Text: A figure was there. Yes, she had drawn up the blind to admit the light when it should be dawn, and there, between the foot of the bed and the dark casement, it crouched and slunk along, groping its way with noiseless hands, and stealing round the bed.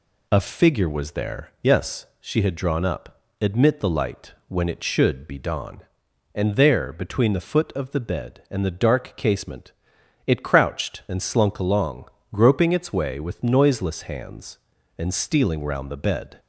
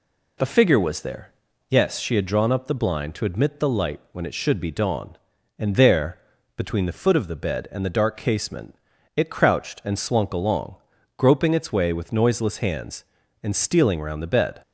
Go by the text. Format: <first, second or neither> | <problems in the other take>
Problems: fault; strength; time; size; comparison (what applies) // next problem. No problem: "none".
second | skips "the blind to"; at 3.2 s // pauses between "light" and "when"; slight; at 4.3 s; 0.16 s long